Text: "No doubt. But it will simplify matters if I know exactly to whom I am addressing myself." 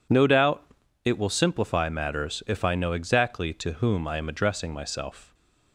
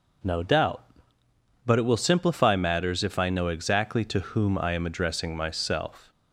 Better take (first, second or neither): second